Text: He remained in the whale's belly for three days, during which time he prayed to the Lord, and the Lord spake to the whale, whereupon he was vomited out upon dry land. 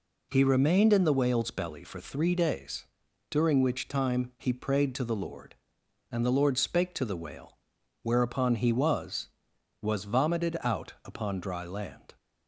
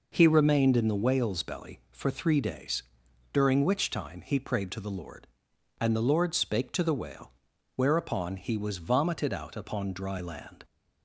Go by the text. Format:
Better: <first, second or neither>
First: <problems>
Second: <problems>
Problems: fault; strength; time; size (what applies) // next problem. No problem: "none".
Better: second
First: says "was" twice; at 9.7 s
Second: none